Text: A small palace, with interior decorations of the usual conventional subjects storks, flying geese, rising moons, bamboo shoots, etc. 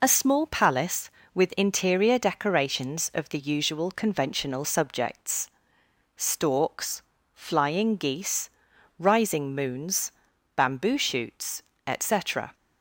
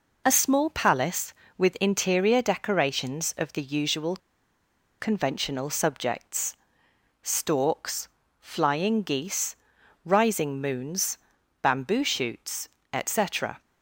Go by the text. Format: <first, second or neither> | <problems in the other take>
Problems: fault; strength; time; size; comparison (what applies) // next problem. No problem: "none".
first | pauses between "usual" and "conventional"; noticeable; at 4.1 s; 0.82 s long // pauses between "subjects" and "storks"; noticeable; at 6.5 s; 0.66 s long; noticeable in the first